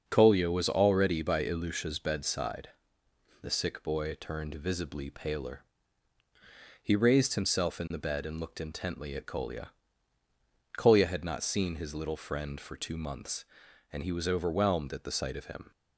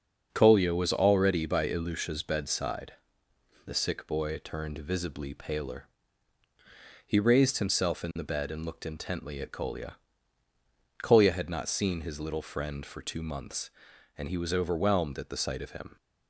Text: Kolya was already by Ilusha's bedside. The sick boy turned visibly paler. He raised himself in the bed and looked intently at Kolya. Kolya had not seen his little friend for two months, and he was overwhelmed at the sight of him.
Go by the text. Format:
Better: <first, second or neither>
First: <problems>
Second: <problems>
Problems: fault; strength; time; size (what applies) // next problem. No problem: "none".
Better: neither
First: starts louder than the rest; until 1.0 s; 6.5 dB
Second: starts louder than the rest; until 1.3 s; 6.5 dB